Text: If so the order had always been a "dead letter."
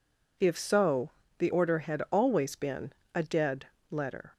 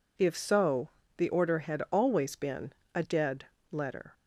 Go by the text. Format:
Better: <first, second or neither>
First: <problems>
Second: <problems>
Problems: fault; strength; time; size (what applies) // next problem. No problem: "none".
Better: neither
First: pauses between "so" and "the"; slight; at 1.1 s; 0.26 s long // pauses between "been" and "a"; slight; at 2.9 s; 0.22 s long // pauses between "dead" and "letter"; slight; at 3.6 s; 0.22 s long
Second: pauses between "so" and "the"; slight; at 0.9 s; 0.26 s long // pauses between "been" and "a"; slight; at 2.7 s; 0.22 s long // pauses between "dead" and "letter"; slight; at 3.4 s; 0.24 s long